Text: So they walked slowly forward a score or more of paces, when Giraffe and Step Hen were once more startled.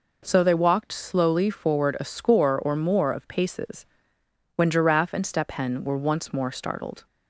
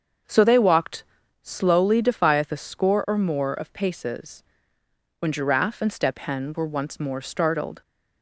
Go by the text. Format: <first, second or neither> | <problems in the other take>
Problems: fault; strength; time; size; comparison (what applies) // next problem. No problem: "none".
first | starts louder than the rest; until 1.6 s; 6.5 dB // pauses between "walked" and "slowly"; at 1.0 s; 0.40 s long // says "defieth" for "forward"; at 2.0 s